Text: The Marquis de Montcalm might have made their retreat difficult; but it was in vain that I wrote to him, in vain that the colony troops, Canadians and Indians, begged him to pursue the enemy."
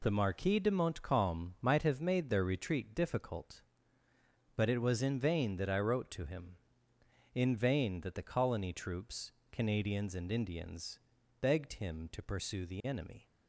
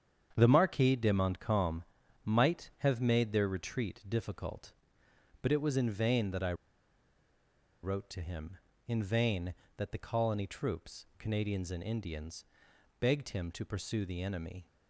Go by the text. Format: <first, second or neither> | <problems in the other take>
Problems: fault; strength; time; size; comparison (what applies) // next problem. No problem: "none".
first | starts louder than the rest; strong; until 1.3 s; 8 dB // pauses between "Montcalm" and "might"; at 1.8 s; 0.40 s long // pauses between "I" and "wrote"; strong; at 6.5 s; 1.2 s long